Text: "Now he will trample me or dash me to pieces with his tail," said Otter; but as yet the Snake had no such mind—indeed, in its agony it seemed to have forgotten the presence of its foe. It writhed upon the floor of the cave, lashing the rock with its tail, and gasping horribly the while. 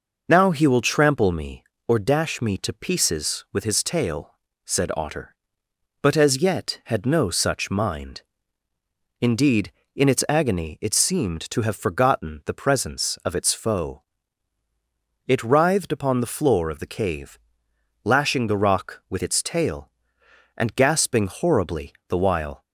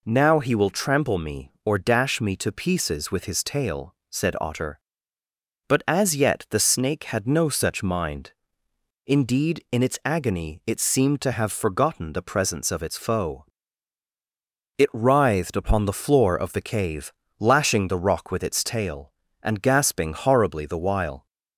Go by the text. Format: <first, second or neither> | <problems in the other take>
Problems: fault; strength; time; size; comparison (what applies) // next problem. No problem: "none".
second | skips "the Snake"; at 6.8 s